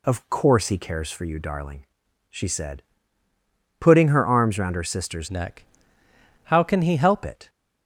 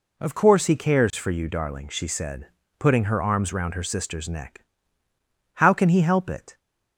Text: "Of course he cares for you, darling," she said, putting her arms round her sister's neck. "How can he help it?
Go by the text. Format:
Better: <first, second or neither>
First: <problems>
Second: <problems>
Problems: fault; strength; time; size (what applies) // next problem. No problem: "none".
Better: second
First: changes voice from "neck" to "help"; from 5.2 to 7.2 s; 2.0 s long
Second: none